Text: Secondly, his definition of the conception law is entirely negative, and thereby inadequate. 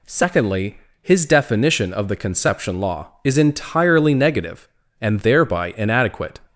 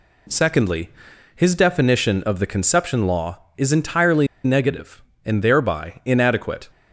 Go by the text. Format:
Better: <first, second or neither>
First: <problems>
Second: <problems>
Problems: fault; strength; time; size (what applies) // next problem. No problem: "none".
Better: first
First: none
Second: pauses between "entirely" and "negative"; slight; at 4.2 s; 0.18 s long